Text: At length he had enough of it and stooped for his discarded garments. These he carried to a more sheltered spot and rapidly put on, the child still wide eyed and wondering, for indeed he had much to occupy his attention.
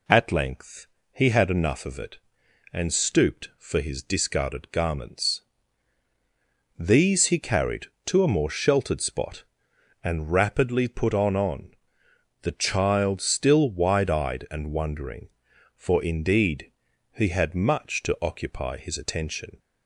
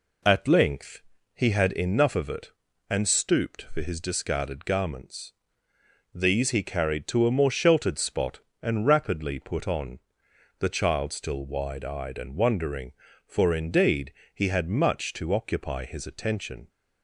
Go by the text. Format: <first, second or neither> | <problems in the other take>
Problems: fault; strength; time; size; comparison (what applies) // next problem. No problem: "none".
second | pauses between "length" and "he"; slight; at 0.8 s; 0.26 s long; slight in the second // says "on" twice; at 11.3 s // pauses between "indeed" and "he"; at 16.7 s; 0.42 s long; slight in the second